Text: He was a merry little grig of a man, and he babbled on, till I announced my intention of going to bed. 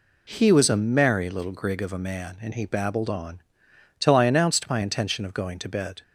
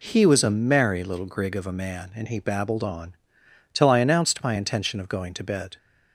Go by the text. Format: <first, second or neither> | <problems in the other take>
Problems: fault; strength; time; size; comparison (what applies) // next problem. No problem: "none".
neither | none